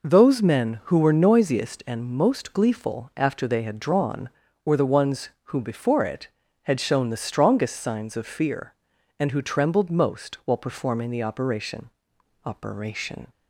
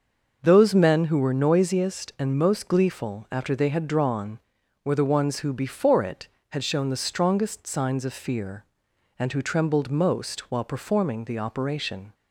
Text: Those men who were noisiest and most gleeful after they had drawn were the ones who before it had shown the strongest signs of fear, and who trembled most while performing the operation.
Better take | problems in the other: second | says "operation" twice; at 12.4 s

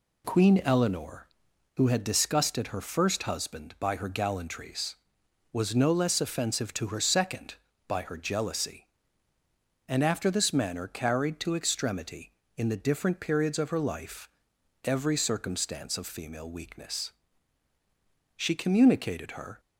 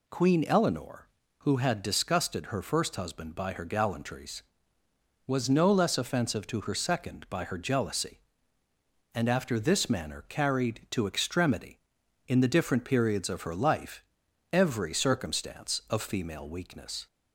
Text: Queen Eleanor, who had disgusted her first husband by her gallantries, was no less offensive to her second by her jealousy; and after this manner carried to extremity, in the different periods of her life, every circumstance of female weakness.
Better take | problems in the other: second | goes on to say "She communicated her"; noticeable; from 18.3 s on; 1.2 s long

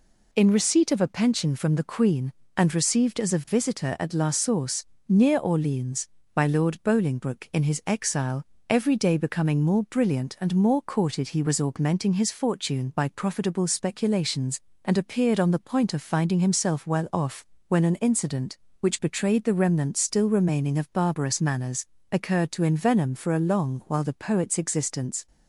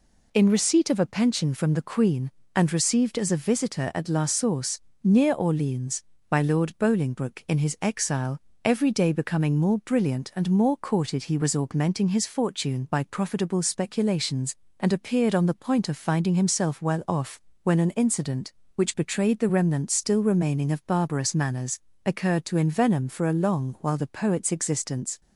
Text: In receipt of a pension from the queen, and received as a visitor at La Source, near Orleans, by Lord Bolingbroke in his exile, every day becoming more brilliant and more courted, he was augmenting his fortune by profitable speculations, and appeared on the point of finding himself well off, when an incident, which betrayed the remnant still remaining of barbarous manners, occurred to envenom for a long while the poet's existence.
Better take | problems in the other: neither | none

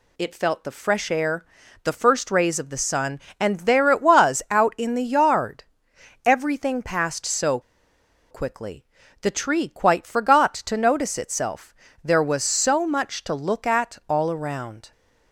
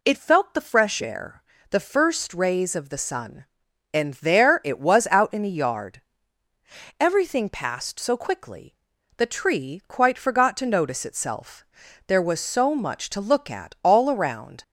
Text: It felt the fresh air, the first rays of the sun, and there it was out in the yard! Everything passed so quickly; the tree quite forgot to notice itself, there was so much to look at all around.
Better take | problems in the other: second | pauses between "so" and "quickly"; noticeable; at 7.5 s; 0.70 s long

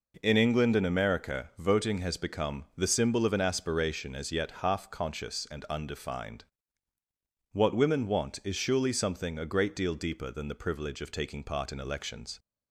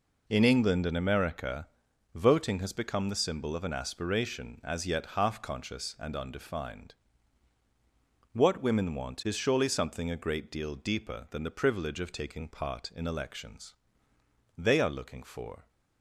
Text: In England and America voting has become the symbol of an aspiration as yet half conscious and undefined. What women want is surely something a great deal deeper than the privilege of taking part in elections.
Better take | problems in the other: first | pauses between "America" and "voting"; noticeable; at 1.6 s; 0.46 s long // goes on to say "They are looking for"; noticeable; from 14.5 s on; 1.1 s long

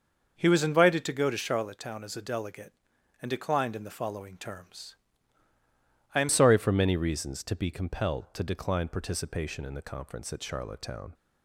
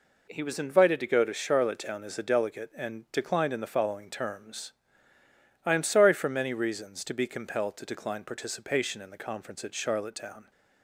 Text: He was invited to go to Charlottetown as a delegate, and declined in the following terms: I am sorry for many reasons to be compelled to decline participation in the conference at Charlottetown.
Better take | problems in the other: second | starts louder than the rest; until 1.3 s; 6 dB // changes voice at "sorry"; from 6.2 s on; 4.9 s long

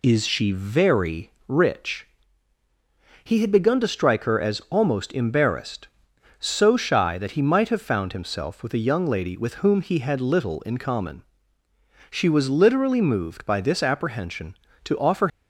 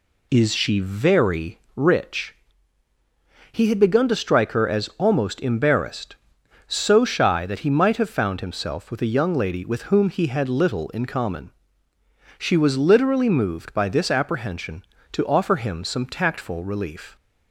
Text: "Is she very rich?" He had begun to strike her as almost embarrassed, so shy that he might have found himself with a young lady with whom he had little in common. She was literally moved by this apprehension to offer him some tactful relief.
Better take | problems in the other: second | pauses between "very" and "rich"; slight; at 1.2 s; 0.16 s long; slight in the second // stops before "him some tactful relief"; at 15.2 s

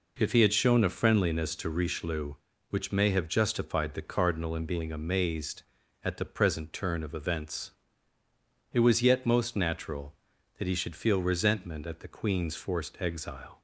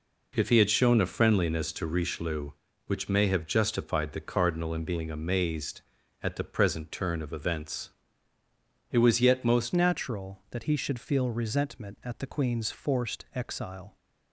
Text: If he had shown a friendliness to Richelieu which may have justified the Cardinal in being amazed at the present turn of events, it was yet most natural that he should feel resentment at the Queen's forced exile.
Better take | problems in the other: first | changes voice at "natural"; from 9.7 s on; 4.2 s long

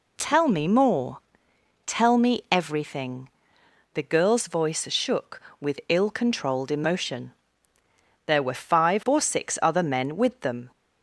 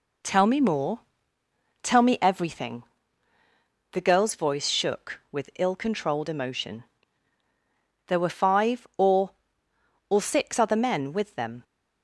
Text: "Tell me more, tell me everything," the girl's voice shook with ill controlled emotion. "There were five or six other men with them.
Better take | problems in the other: first | says "or" twice; at 10.1 s

